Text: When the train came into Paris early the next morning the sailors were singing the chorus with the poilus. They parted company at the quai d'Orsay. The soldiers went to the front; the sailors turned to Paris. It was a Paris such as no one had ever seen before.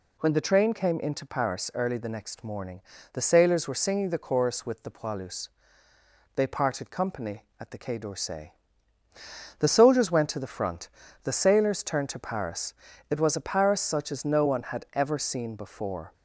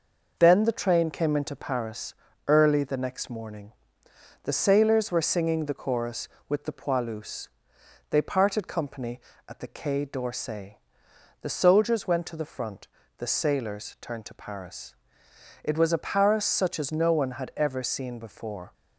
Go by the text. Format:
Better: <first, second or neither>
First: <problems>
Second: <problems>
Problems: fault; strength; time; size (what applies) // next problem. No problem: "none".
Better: first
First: pauses between "morning" and "the"; slight; at 2.8 s; 0.30 s long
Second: says "Then" for "When"; at 0.3 s // pauses between "Paris" and "early"; slight; at 2.1 s; 0.34 s long // pauses between "morning" and "the"; noticeable; at 3.7 s; 0.72 s long